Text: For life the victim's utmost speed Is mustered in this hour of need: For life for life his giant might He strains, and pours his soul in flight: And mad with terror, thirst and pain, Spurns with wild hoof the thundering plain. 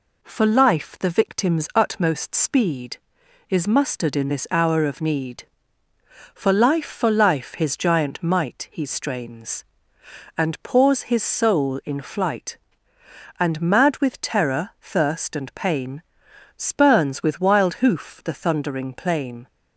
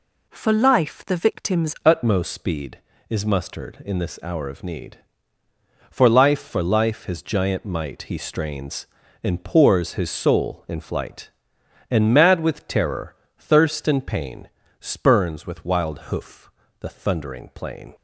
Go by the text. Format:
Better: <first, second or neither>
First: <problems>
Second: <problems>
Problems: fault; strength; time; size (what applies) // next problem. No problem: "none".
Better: first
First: none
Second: changes voice at "utmost"; from 1.8 s on; 16.1 s long // pauses between "wild" and "hoof"; slight; at 15.9 s; 0.16 s long // pauses between "hoof" and "the"; slight; at 16.5 s; 0.28 s long